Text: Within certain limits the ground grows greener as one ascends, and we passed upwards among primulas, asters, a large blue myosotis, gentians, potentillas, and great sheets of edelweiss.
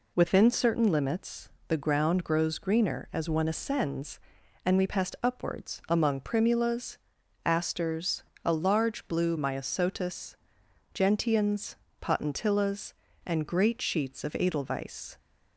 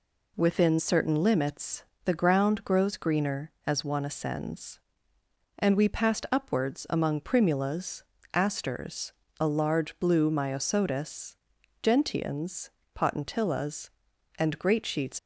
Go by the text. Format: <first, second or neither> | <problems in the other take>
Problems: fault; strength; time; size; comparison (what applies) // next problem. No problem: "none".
first | pauses between "limits" and "the"; slight; at 1.8 s; 0.22 s long; slight in the first // stops before "of edelweiss"; at 15.1 s